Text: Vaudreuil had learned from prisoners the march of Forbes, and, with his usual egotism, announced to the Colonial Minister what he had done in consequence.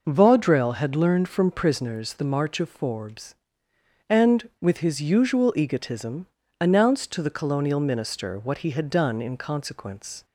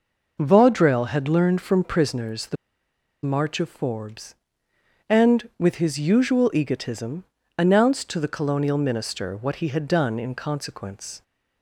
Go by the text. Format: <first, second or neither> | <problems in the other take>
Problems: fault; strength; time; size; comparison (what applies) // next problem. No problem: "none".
first | pauses between "the" and "march"; noticeable; at 2.5 s; 0.68 s long